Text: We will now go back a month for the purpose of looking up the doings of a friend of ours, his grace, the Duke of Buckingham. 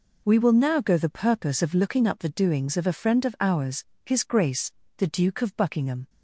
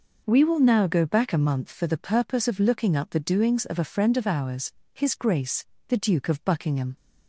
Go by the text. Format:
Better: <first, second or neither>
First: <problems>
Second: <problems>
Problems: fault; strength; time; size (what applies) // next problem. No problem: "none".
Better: second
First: skips "back a month for"; at 0.9 s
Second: none